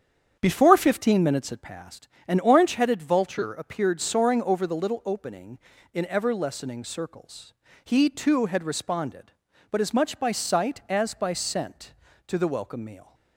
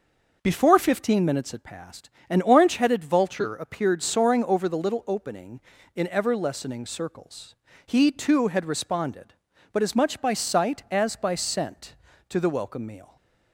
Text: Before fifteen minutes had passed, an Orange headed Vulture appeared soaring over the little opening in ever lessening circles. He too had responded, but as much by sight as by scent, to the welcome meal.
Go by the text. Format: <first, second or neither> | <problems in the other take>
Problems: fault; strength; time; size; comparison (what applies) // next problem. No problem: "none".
second | starts louder than the rest; strong; until 2.0 s; 8 dB